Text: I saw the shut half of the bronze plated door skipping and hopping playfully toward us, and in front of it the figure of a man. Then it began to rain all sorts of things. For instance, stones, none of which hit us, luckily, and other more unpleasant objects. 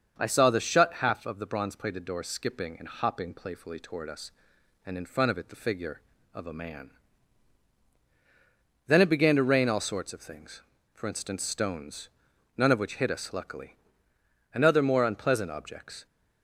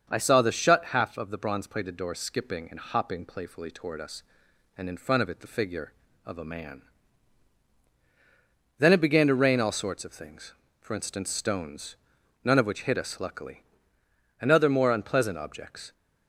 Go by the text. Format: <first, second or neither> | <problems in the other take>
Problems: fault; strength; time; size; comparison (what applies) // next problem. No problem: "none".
neither | starts louder than the rest; the same in both